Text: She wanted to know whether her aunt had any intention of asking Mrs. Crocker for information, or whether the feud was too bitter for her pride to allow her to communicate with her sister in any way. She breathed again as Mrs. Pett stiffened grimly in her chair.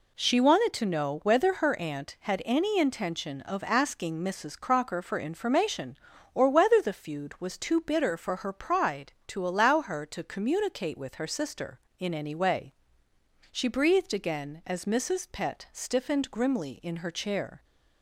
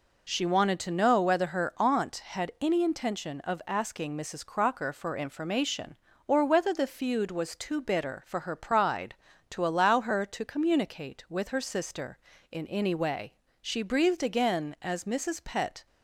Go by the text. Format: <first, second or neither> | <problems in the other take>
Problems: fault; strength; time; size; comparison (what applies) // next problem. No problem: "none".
first | stops before "stiffened grimly in her chair"; at 15.8 s